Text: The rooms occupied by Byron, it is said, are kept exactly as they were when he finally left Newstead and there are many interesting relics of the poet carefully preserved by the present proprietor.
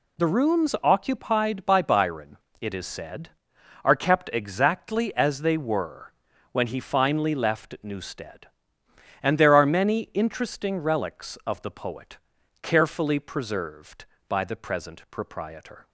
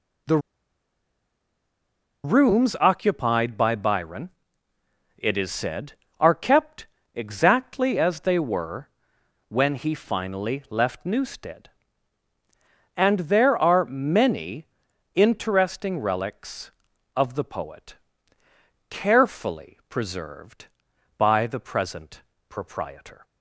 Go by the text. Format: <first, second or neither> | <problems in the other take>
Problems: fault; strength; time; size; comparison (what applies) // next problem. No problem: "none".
first | pauses between "The" and "rooms"; strong; at 0.3 s; 1.8 s long // pauses between "kept" and "exactly"; slight; at 6.8 s; 0.28 s long // pauses between "were" and "when"; noticeable; at 8.8 s; 0.60 s long; also in the first // pauses between "many" and "interesting"; noticeable; at 14.6 s; 0.48 s long // pauses between "poet" and "carefully"; noticeable; at 17.9 s; 0.96 s long; also in the first // pauses between "present" and "proprietor"; slight; at 22.2 s; 0.28 s long